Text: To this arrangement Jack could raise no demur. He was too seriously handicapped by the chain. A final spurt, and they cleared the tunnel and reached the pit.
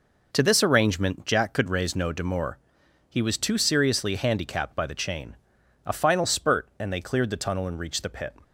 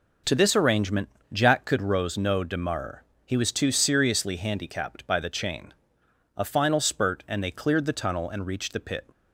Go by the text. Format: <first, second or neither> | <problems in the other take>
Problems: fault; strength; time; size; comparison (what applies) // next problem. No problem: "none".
first | pauses between "arrangement" and "Jack"; slight; at 1.0 s; 0.24 s long // says "rose" for "raise"; at 1.8 s